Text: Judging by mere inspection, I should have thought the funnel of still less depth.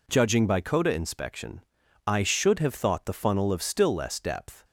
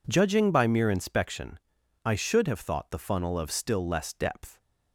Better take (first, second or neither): second